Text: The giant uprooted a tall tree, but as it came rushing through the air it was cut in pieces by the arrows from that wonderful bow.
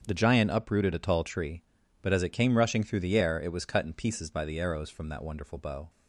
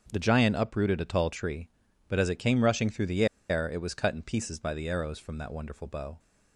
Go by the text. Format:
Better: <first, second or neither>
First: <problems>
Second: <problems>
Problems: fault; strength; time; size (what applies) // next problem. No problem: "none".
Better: first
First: starts louder than the rest; until 1.1 s; 7 dB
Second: starts louder than the rest; until 1.1 s; 7 dB // pauses between "the" and "air"; slight; at 3.2 s; 0.24 s long